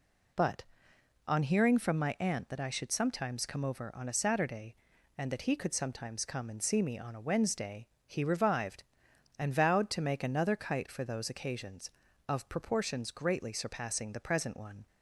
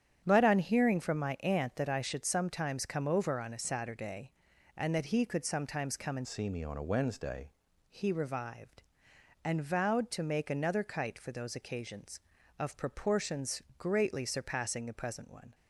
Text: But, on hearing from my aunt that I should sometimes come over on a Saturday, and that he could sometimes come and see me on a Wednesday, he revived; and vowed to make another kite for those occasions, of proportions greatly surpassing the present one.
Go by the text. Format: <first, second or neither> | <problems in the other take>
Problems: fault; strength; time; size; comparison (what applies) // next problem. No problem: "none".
first | starts louder than the rest; strong; until 1.2 s; 9 dB // changes voice from "see" to "Wednesday"; from 6.2 to 7.5 s; 1.3 s long // pauses between "proportions" and "greatly"; slight; at 13.6 s; 0.16 s long